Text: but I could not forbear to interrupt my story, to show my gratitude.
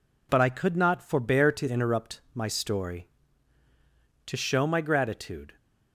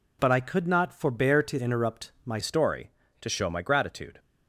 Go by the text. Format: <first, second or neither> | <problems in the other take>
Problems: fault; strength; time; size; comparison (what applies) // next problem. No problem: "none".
first | changes voice at "story"; from 2.4 s on; 1.7 s long